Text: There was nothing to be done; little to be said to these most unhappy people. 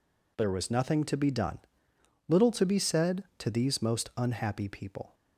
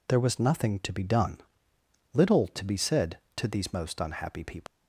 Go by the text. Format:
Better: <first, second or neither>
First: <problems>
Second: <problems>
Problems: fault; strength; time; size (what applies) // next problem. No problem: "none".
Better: first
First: none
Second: leaves "people" unfinished; at 4.6 s; 75 ms